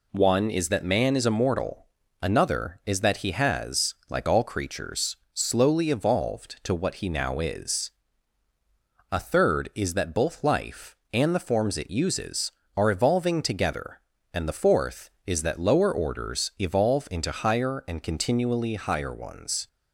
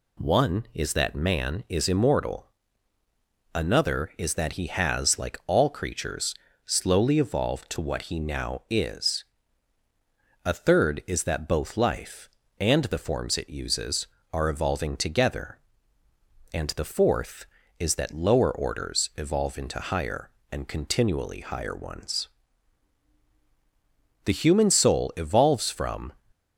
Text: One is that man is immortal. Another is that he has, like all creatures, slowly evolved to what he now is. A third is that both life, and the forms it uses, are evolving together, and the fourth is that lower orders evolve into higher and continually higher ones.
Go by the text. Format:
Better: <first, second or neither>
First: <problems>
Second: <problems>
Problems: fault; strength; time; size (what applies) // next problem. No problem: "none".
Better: first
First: none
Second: goes on to say "The human soul evolves from"; strong; from 24.2 s on; 1.8 s long